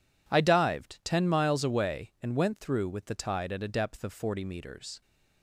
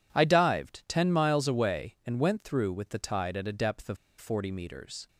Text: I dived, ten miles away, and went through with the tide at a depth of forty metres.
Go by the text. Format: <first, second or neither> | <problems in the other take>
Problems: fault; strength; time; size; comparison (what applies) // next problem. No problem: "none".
first | pauses between "of" and "forty"; slight; at 3.9 s; 0.22 s long